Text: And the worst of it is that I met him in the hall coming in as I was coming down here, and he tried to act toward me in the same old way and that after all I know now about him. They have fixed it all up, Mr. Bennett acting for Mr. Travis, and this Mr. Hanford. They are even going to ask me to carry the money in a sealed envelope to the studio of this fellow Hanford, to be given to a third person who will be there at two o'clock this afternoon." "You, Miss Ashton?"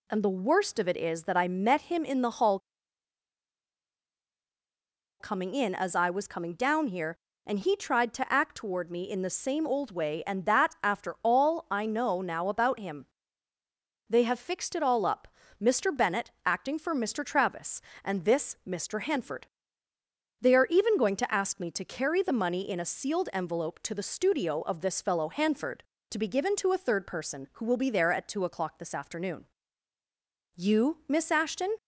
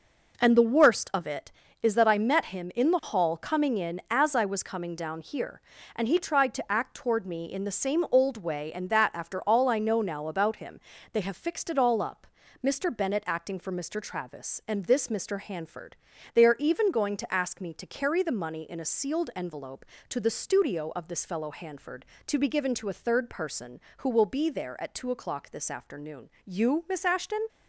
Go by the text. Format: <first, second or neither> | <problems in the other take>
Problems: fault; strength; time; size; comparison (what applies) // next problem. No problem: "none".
second | pauses between "hall" and "coming"; strong; at 2.5 s; 2.6 s long // pauses between "Bennett" and "acting"; slight; at 16.2 s; 0.16 s long